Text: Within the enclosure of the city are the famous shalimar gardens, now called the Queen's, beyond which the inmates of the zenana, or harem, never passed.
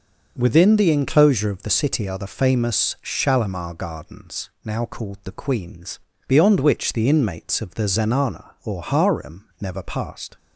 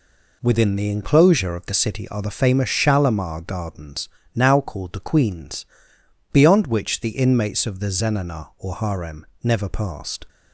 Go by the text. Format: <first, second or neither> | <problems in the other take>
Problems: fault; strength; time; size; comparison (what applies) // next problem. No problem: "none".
neither | none